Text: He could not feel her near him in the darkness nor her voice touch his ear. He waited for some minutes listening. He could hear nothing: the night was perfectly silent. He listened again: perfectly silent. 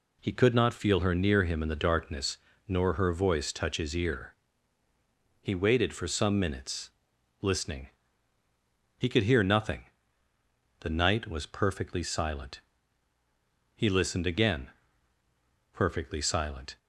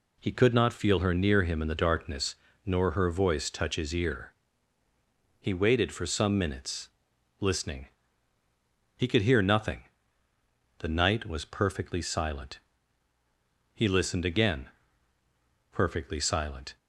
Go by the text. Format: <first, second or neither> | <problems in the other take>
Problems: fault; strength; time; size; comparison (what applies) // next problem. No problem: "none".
neither | pauses between "darkness" and "nor"; slight; the same in both // pauses between "minutes" and "listening"; noticeable; the same in both